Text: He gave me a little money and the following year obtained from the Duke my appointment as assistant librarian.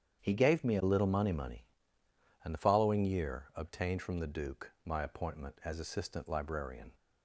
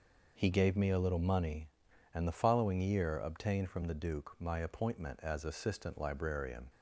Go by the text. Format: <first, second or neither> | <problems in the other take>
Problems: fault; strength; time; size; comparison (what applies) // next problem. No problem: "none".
second | starts louder than the rest; strong; until 1.2 s; 8.5 dB // says "money" twice; at 1.3 s